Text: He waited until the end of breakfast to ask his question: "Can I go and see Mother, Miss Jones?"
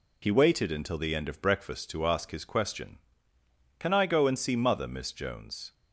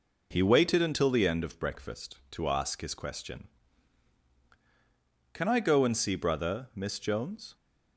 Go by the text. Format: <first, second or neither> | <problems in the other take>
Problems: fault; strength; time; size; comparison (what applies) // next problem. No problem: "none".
first | says "Brother" for "Mother"; at 6.1 s